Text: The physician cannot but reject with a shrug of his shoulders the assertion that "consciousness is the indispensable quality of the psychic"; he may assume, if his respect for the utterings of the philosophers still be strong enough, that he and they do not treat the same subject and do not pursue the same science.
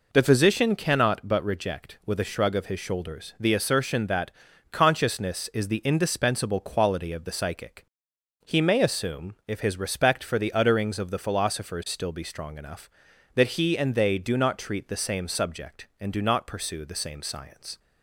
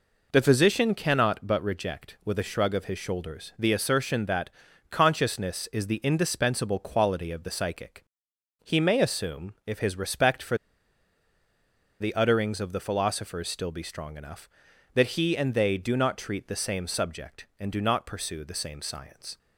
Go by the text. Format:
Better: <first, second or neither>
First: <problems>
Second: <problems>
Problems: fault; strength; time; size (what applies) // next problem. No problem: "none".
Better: first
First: pauses between "that" and "consciousness"; at 4.3 s; 0.40 s long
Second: pauses between "that" and "consciousness"; at 4.4 s; 0.40 s long // pauses between "for" and "the"; strong; at 10.5 s; 1.4 s long